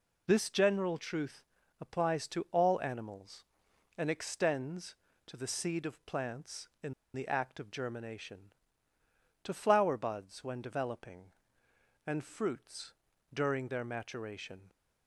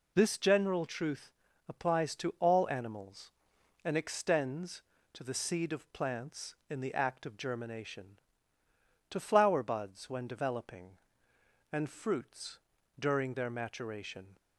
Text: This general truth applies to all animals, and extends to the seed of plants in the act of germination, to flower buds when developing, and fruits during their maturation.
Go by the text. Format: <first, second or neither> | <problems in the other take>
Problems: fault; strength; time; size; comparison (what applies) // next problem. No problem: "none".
second | pauses between "truth" and "applies"; slight; at 1.4 s; 0.36 s long; slight in the second // pauses between "in" and "the"; slight; at 6.9 s; 0.22 s long // pauses between "fruits" and "during"; at 12.9 s; 0.40 s long; also in the second